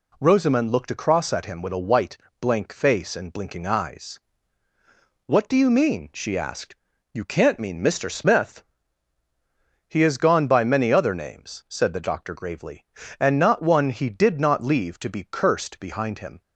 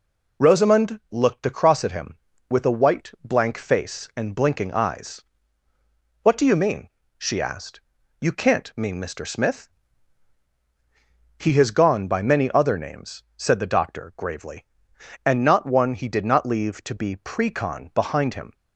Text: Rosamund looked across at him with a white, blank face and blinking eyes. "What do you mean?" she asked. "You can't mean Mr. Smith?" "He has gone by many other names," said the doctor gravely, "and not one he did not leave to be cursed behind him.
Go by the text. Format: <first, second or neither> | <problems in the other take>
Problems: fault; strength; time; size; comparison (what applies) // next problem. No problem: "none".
first | says "precon" for "cursed"; at 17.1 s